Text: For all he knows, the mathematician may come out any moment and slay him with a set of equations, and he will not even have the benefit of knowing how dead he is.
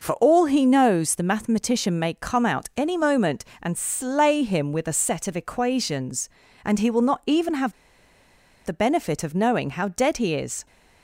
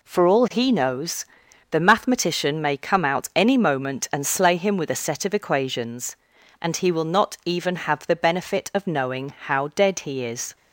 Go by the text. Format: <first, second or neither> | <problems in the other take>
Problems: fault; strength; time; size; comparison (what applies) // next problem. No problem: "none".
second | pauses between "have" and "the"; noticeable; at 7.7 s; 0.91 s long